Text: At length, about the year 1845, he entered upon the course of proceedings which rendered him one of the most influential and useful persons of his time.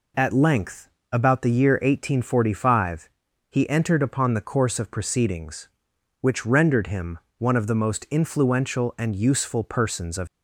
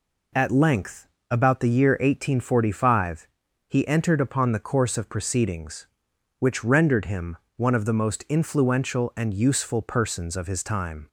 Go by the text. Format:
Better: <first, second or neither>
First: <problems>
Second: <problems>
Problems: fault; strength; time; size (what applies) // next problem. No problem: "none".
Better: second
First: pauses between "him" and "one"; slight; at 7.1 s; 0.18 s long // stops before "his time"; at 10.2 s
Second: pauses between "him" and "one"; slight; at 7.3 s; 0.18 s long